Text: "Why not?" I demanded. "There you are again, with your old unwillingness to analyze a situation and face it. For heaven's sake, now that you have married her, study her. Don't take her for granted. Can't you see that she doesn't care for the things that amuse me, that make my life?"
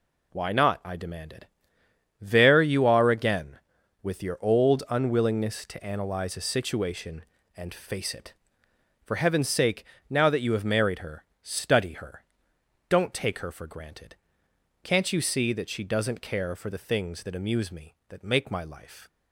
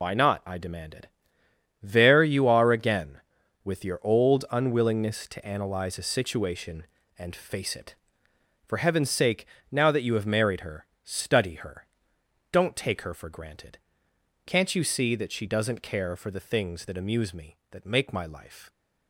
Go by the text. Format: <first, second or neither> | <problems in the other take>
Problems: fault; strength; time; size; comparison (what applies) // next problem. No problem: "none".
first | loses the start of "Why"; at 0.0 s; 75 ms